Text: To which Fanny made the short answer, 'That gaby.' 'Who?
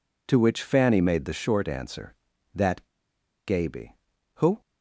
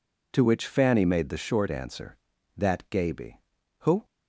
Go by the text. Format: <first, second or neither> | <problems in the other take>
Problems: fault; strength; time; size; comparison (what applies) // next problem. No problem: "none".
second | pauses between "That" and "gaby"; noticeable; at 2.8 s; 0.59 s long